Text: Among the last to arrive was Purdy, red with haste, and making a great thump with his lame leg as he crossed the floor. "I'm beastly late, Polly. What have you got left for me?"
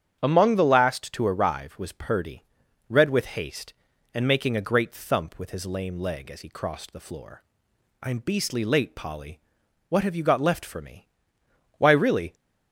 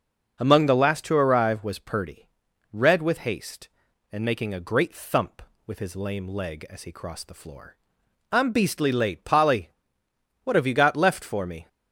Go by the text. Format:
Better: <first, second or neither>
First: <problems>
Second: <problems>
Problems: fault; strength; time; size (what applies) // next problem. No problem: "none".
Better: second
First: starts louder than the rest; strong; until 1.2 s; 9 dB // goes on to say "Why really"; from 11.7 s on; 0.58 s long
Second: starts louder than the rest; until 1.4 s; 6.5 dB